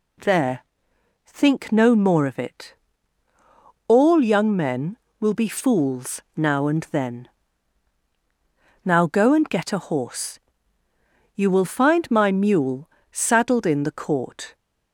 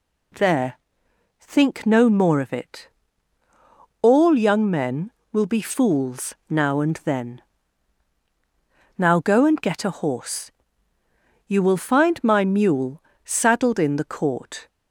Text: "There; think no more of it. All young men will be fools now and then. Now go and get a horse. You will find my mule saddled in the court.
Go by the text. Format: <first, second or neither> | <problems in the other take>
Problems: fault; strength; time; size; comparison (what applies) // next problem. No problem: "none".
neither | pauses between "mule" and "saddled"; slight; the same in both